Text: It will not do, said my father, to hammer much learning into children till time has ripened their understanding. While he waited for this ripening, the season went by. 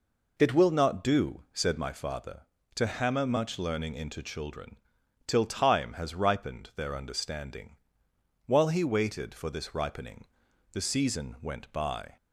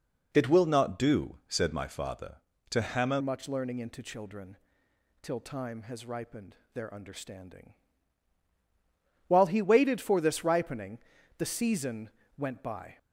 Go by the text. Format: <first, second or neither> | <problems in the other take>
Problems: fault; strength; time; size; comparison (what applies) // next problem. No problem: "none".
first | changes voice at "much"; from 3.1 s on; 9.8 s long // pauses between "children" and "till"; noticeable; at 4.5 s; 0.66 s long; noticeable in the first // pauses between "ripened" and "their"; slight; at 6.5 s; 0.18 s long // pauses between "season" and "went"; slight; at 12.0 s; 0.28 s long